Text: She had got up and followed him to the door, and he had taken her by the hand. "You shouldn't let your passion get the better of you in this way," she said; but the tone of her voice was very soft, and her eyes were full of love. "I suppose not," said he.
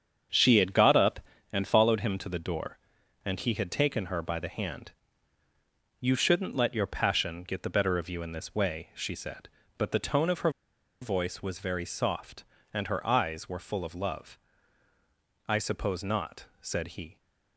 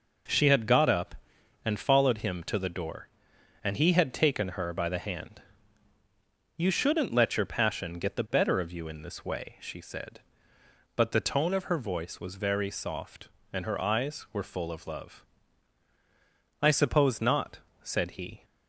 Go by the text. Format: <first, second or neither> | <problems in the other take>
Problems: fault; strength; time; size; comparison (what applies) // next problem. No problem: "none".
second | starts louder than the rest; strong; until 1.6 s; 7.5 dB // pauses between "her" and "voice"; noticeable; at 10.5 s; 0.50 s long